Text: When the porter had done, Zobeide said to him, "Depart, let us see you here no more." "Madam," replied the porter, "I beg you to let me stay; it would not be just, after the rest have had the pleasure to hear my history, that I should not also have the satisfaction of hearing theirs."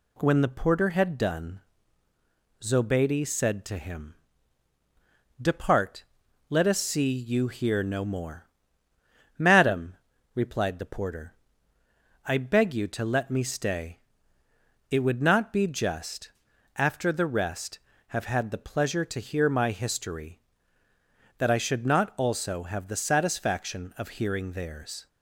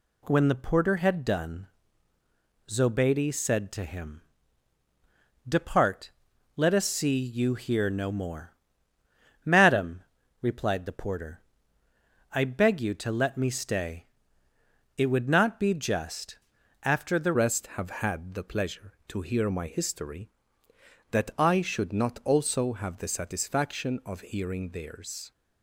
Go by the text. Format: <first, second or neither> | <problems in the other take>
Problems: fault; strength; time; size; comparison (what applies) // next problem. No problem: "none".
first | changes voice at "rest"; from 17.3 s on; 8.0 s long